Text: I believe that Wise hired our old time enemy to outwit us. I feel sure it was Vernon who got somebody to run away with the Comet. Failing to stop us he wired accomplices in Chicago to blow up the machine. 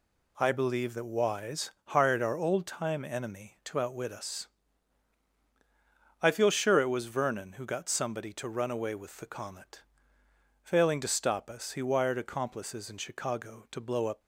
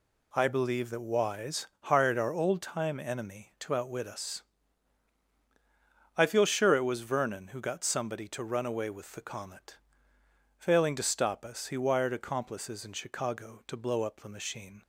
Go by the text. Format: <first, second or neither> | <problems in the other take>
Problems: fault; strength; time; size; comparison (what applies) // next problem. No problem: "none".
second | pauses between "Wise" and "hired"; slight; at 1.6 s; 0.18 s long; slight in the second // stops before "the machine"; at 14.2 s